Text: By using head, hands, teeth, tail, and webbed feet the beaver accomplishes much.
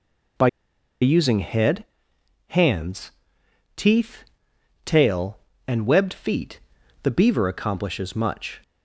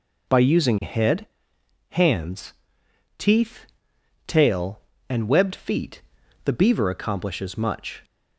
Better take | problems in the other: second | pauses between "By" and "using"; noticeable; at 0.4 s; 0.53 s long // pauses between "feet" and "the"; at 6.6 s; 0.42 s long; also in the second

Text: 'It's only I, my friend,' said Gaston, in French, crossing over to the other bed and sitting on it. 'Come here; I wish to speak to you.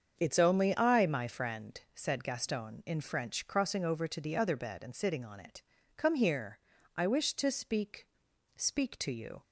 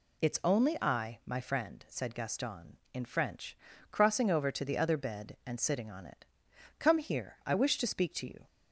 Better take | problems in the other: second | starts louder than the rest; strong; until 1.2 s; 7 dB // says "speak" twice; at 8.5 s

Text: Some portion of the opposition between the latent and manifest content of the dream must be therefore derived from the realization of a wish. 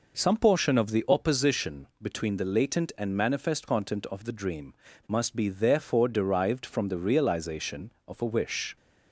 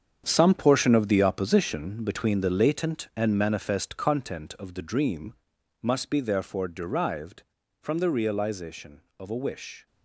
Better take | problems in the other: first | gets quieter; strong; throughout; 10.5 dB // pauses between "dream" and "must"; noticeable; at 5.3 s; 0.48 s long; slight in the first

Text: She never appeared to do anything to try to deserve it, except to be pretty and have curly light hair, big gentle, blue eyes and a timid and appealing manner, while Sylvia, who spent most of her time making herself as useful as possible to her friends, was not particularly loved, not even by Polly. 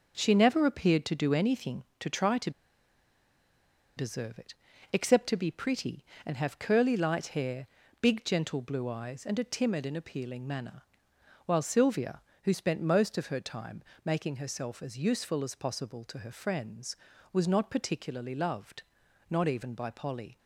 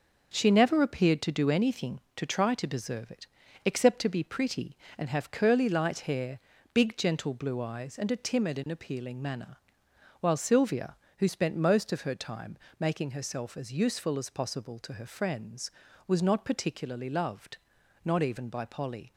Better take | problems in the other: second | starts louder than the rest; until 1.2 s; 6.5 dB; also in the second // pauses between "to" and "deserve"; strong; at 2.4 s; 1.4 s long // pauses between "time" and "making"; slight; at 13.8 s; 0.22 s long; slight in the second

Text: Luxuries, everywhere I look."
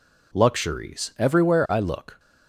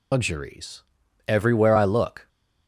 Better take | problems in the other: first | loses the start of "Luxuries"; at 0.1 s; 160 ms

